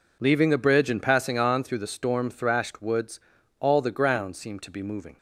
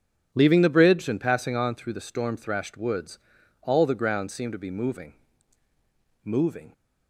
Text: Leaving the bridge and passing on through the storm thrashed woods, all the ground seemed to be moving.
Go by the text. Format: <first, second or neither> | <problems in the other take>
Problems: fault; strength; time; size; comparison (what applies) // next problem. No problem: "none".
first | says "moving" twice; at 6.2 s